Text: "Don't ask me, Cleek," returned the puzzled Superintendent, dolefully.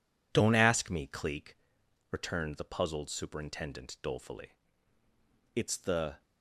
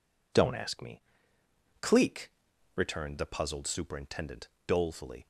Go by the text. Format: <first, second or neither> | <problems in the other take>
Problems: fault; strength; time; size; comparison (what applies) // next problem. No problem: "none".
second | goes on to say "It's the"; noticeable; from 5.5 s on; 0.68 s long